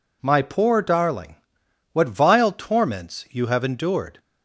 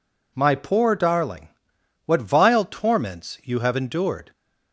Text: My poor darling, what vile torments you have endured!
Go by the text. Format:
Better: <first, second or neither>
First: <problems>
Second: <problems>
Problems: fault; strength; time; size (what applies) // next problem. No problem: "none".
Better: neither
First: none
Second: none